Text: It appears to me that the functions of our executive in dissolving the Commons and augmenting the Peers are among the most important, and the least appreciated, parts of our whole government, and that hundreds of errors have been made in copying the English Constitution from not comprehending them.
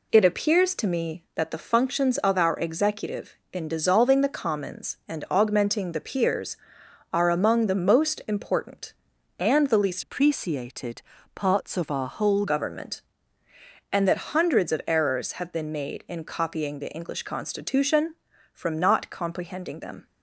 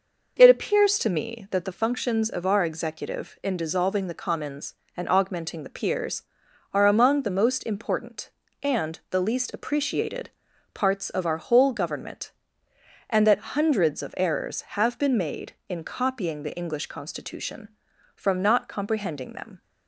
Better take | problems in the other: second | changes voice from "appreciated" to "whole"; from 10.0 to 12.4 s; 2.4 s long

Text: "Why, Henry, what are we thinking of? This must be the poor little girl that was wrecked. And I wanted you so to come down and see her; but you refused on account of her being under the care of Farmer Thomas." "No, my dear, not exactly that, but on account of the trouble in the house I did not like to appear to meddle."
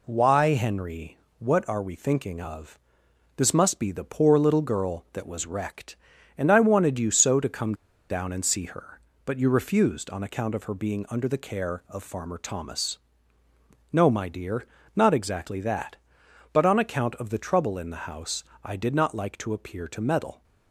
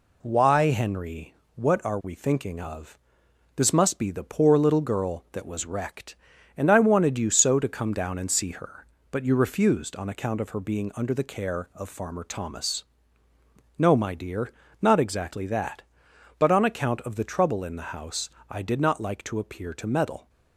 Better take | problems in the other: second | pauses between "come" and "down"; at 7.7 s; 0.36 s long // pauses between "house" and "I"; slight; at 18.4 s; 0.20 s long; slight in the second

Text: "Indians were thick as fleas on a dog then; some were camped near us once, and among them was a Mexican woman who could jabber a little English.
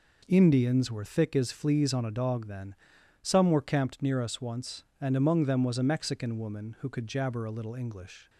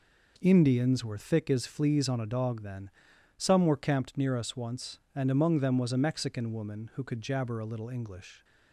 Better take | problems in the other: neither | none

